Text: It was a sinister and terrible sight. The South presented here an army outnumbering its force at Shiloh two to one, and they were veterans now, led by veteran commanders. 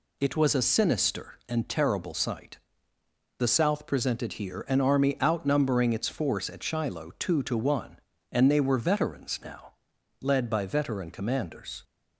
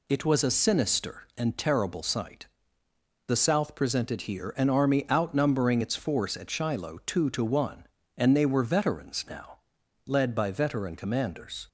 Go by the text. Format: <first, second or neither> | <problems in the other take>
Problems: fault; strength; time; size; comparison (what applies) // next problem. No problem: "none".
neither | none